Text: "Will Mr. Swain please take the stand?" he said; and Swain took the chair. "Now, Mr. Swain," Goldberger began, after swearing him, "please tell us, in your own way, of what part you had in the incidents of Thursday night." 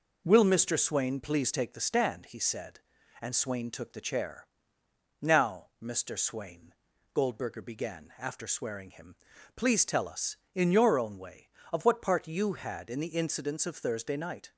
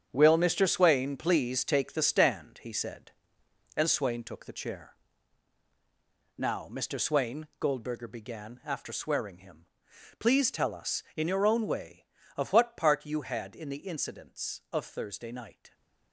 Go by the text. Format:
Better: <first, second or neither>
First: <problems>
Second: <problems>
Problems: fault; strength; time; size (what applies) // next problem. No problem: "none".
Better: first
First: none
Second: gets quieter; strong; throughout; 10 dB